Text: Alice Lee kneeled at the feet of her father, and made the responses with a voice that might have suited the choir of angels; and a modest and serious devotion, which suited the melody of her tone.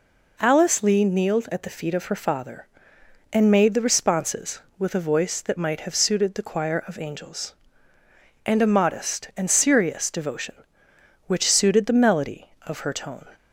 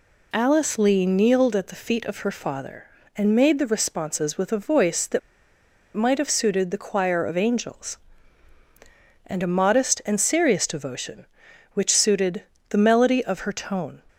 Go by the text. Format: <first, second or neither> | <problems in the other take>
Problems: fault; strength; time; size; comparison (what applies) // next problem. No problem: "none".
first | pauses between "that" and "might"; noticeable; at 5.1 s; 0.75 s long // pauses between "suited" and "the"; slight; at 12.4 s; 0.28 s long